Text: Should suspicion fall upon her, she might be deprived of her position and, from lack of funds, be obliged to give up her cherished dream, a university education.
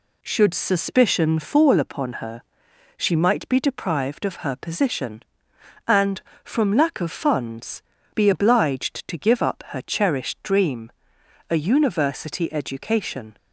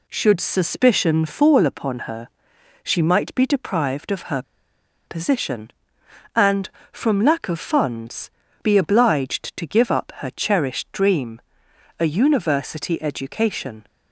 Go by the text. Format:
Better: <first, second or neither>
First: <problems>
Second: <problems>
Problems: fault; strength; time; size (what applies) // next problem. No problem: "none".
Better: first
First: none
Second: pauses between "her" and "position"; noticeable; at 4.4 s; 0.64 s long